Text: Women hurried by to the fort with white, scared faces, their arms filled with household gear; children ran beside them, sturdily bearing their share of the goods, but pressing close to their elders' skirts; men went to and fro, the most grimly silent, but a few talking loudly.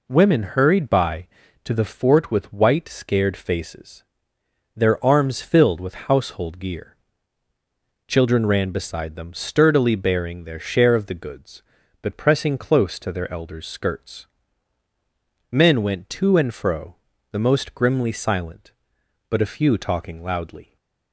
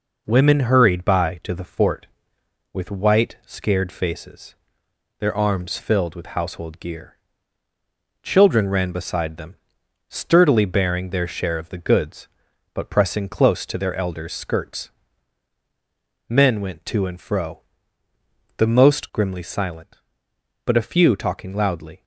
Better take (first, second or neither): neither